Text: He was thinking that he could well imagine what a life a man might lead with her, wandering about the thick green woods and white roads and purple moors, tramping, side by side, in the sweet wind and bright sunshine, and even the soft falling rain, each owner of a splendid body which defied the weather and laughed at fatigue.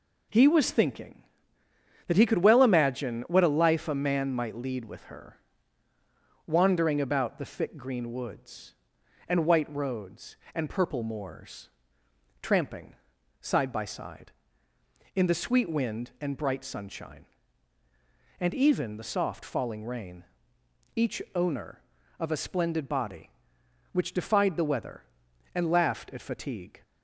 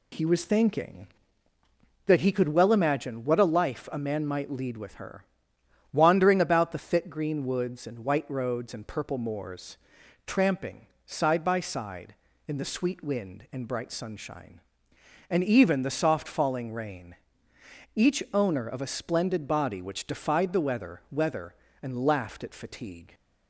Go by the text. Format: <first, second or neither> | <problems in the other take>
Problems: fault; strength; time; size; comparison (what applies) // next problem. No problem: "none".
first | says "weather" twice; at 21.0 s